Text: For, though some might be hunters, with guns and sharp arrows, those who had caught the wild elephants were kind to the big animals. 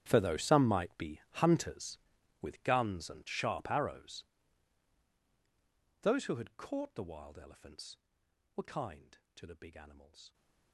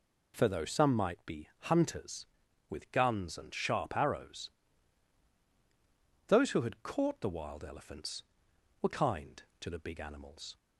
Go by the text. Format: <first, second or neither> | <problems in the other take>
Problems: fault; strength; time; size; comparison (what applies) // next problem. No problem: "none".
second | gets quieter; strong; throughout; 20.5 dB